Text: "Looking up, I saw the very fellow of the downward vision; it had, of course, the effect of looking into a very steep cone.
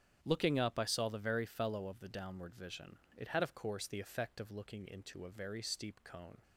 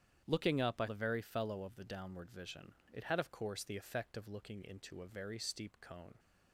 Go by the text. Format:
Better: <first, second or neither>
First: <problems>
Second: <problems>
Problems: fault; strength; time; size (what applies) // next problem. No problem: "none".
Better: first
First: starts louder than the rest; strong; until 1.2 s; 9 dB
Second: starts louder than the rest; strong; until 1.2 s; 9 dB // skips "saw"; at 0.8 s